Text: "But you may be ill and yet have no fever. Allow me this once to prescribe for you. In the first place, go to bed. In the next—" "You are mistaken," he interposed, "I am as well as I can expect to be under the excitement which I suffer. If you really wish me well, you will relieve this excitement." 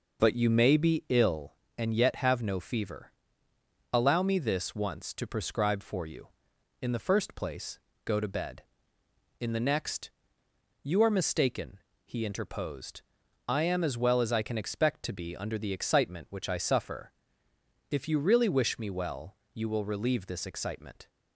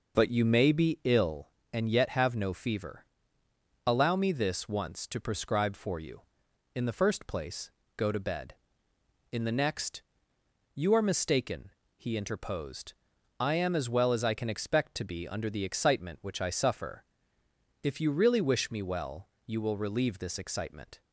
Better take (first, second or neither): neither